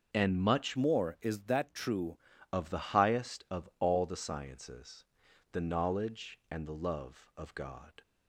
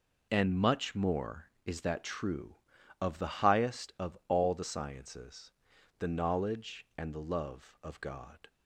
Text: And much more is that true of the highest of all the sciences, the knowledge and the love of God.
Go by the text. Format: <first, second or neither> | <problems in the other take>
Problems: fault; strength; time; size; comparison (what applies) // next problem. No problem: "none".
second | changes voice from "more" to "true"; from 0.7 to 2.1 s; 1.4 s long